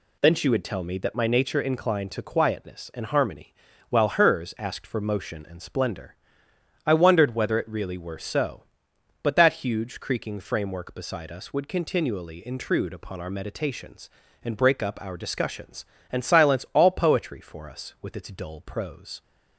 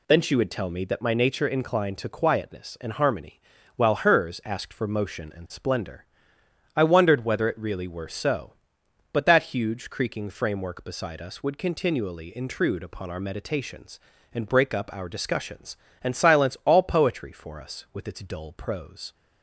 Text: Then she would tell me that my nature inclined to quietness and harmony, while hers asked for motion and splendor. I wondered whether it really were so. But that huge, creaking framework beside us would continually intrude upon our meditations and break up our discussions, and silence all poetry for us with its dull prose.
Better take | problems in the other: neither | none

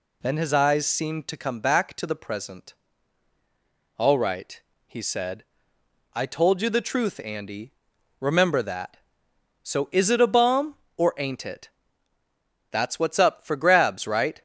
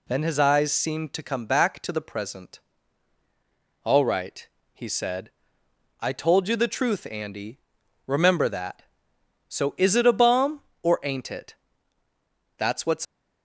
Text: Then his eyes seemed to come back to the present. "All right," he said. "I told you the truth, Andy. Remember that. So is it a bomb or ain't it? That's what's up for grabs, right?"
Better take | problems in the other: first | stops before "up for grabs right"; at 13.0 s

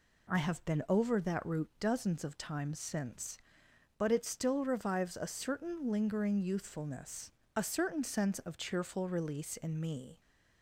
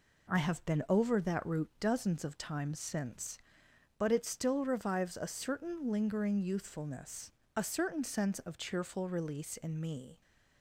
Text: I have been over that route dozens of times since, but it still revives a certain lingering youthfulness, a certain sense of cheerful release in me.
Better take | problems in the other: first | gets quieter; noticeable; throughout; 5.5 dB

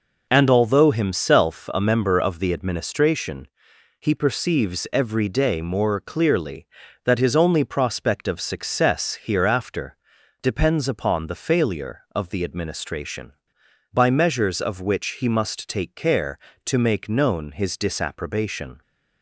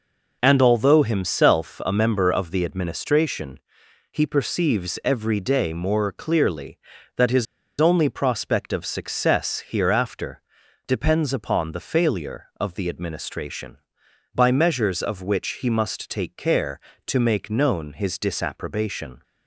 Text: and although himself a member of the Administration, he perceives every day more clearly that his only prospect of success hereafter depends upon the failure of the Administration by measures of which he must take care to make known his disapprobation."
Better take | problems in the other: first | pauses between "his" and "only"; slight; at 7.4 s; 0.35 s long // pauses between "hereafter" and "depends"; noticeable; at 10.4 s; 0.46 s long; noticeable in the first

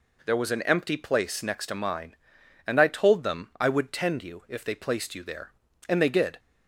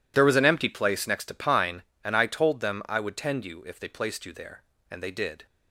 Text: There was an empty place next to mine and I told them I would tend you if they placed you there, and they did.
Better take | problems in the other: first | says "pine" for "mine"; at 1.3 s

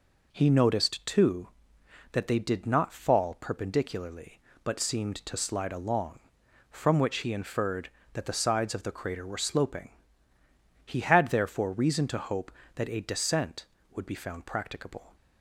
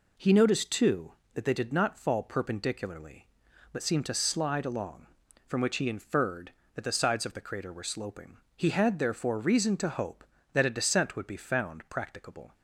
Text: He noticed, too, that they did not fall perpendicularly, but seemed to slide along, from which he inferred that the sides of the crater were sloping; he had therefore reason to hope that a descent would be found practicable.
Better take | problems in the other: neither | none

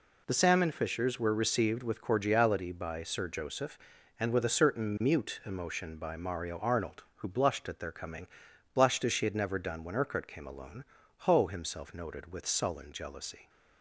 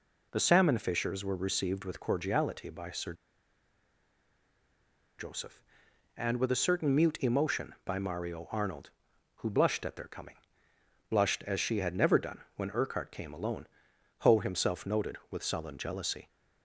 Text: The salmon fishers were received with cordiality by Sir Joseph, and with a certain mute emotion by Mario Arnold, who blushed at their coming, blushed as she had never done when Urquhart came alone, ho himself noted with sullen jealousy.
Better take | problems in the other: first | pauses between "Sir" and "Joseph"; strong; at 3.1 s; 2.0 s long

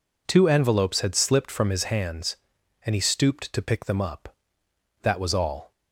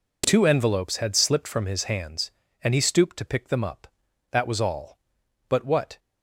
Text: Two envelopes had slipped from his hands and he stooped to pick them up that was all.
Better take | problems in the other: first | goes on to say "But what"; slight; from 5.5 s on; 0.48 s long

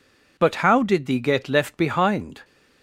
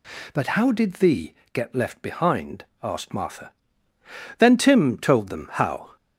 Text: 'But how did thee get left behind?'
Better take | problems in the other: first | pauses between "thee" and "get"; slight; at 1.3 s; 0.18 s long // goes on to say "asked Martha Then Tim told them how"; strong; from 2.8 s on; 3.1 s long

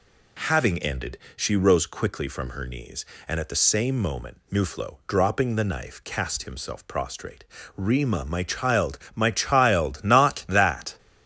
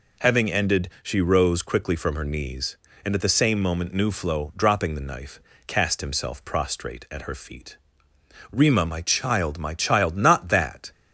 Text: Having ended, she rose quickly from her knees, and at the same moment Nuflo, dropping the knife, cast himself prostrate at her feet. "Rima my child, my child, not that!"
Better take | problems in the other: second | skips "at her feet"; at 7.5 s

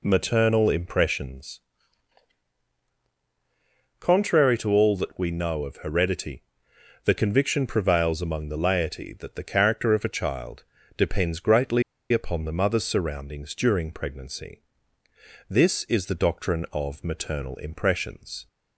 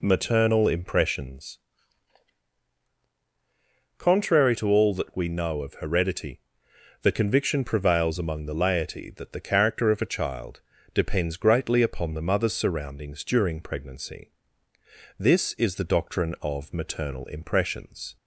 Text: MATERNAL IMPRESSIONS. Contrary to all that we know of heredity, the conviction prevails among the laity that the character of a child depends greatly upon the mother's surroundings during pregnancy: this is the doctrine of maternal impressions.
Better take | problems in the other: second | pauses between "child" and "depends"; slight; at 10.6 s; 0.34 s long; slight in the second // pauses between "greatly" and "upon"; slight; at 11.8 s; 0.30 s long

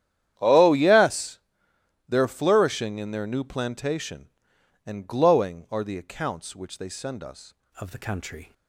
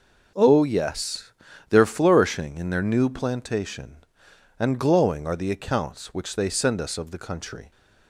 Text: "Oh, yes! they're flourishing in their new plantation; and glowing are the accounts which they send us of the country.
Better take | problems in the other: second | starts louder than the rest; strong; until 1.3 s; 10.5 dB // changes voice at "of"; from 7.7 s on; 0.8 s long

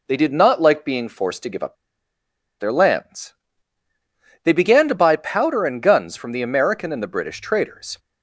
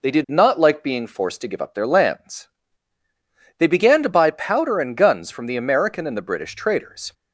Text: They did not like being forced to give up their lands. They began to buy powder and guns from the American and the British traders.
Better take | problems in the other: second | pauses between "up" and "their"; noticeable; at 1.7 s; 0.84 s long

